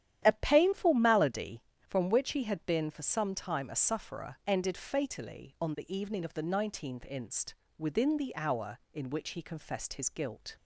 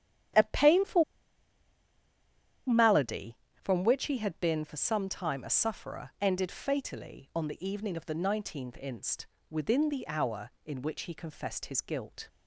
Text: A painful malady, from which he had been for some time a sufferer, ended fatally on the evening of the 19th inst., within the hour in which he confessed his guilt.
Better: first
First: starts louder than the rest; strong; until 1.2 s; 11 dB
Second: starts louder than the rest; strong; until 3.0 s; 11 dB // pauses between "painful" and "malady"; strong; at 1.0 s; 1.6 s long

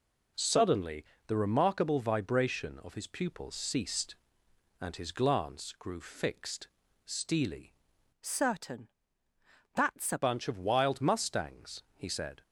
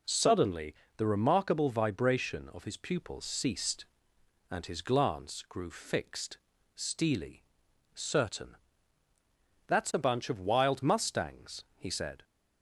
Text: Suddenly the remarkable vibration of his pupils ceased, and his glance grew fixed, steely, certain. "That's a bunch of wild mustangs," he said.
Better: second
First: pauses between "Suddenly" and "the"; slight; at 1.0 s; 0.24 s long // changes voice from "certain" to "a"; from 8.2 to 10.2 s; 2.0 s long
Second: pauses between "Suddenly" and "the"; slight; at 0.7 s; 0.24 s long

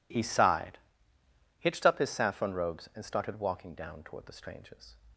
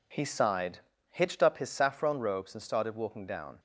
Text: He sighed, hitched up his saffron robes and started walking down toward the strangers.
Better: first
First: none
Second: stops before "toward the strangers"; at 3.5 s

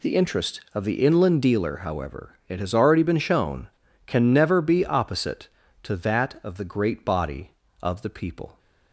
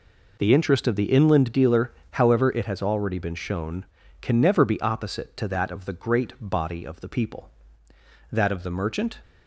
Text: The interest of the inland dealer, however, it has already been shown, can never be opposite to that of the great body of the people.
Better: first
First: none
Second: goes on to say "That of the merchant"; noticeable; from 8.3 s on; 0.90 s long

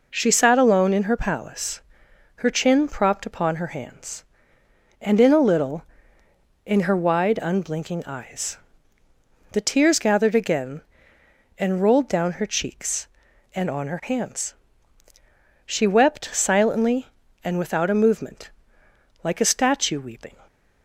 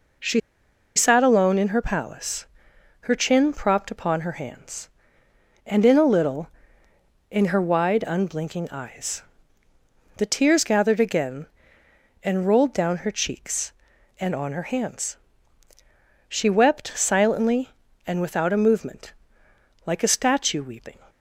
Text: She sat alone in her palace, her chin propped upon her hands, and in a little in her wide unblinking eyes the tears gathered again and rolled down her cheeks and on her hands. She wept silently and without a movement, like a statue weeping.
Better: first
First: pauses between "eyes" and "the"; noticeable; at 8.5 s; 0.94 s long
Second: pauses between "She" and "sat"; noticeable; at 0.4 s; 0.56 s long // pauses between "eyes" and "the"; noticeable; at 9.2 s; 0.94 s long

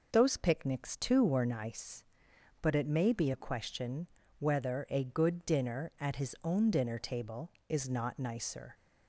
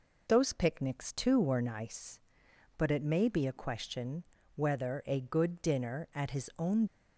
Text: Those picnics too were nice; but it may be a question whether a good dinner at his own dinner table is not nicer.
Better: first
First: pauses between "question" and "whether"; slight; at 4.0 s; 0.32 s long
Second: pauses between "question" and "whether"; slight; at 4.2 s; 0.32 s long // stops before "dinner table is not nicer"; at 6.8 s

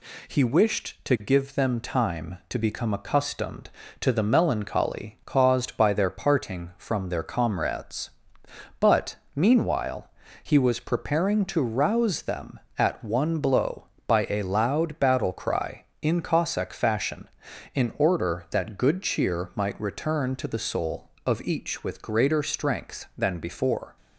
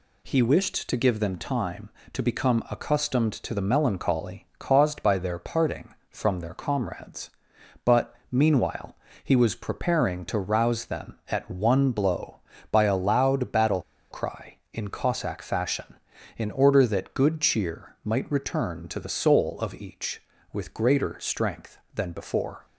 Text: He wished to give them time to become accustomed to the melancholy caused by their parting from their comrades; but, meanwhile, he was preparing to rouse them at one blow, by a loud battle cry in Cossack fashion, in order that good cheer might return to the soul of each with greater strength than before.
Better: first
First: none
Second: pauses between "battle" and "cry"; slight; at 13.8 s; 0.29 s long

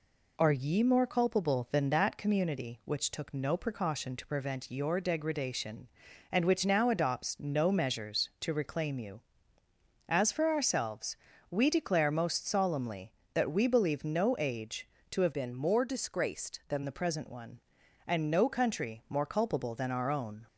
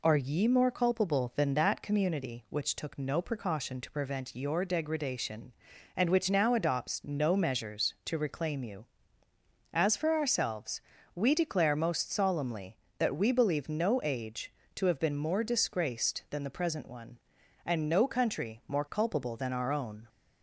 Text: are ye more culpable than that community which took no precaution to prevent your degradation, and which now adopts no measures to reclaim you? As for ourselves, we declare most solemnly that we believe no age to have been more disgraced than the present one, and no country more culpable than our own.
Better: second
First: changes voice from "been" to "than"; from 15.3 to 16.8 s; 1.5 s long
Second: none

